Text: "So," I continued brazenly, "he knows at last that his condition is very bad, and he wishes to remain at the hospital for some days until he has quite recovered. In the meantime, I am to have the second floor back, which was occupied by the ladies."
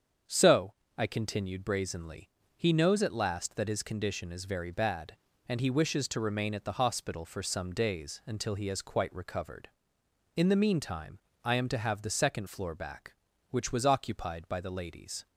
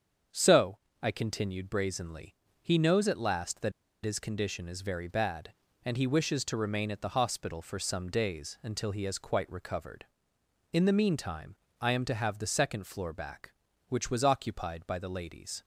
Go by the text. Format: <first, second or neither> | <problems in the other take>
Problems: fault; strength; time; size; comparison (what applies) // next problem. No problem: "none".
first | starts louder than the rest; strong; until 1.5 s; 7.5 dB; strong in the first // pauses between "that" and "his"; slight; at 3.7 s; 0.32 s long